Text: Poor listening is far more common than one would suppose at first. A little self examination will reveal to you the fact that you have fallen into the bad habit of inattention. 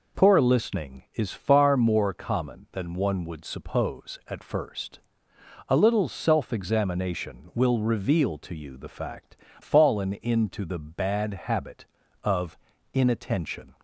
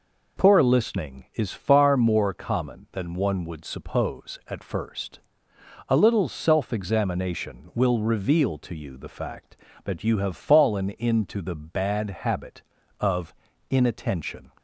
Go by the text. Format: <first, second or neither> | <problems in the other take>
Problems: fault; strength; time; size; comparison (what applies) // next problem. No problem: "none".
second | skips "that you have"; at 9.4 s // pauses between "of" and "inattention"; slight; at 12.5 s; 0.36 s long; slight in the second